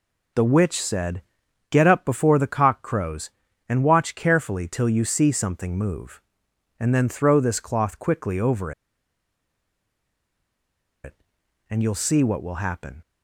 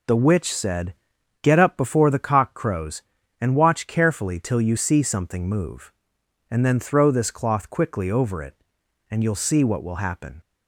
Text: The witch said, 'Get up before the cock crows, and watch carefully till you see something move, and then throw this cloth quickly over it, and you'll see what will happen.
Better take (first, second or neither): second